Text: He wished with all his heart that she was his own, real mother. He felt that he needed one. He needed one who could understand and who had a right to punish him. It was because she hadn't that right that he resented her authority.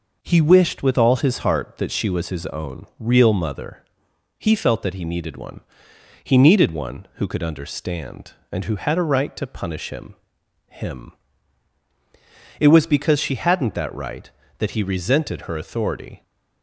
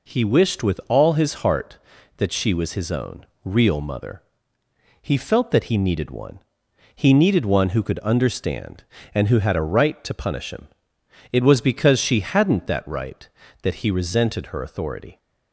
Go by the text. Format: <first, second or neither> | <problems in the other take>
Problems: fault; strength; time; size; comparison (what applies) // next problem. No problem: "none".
second | says "him" twice; at 10.6 s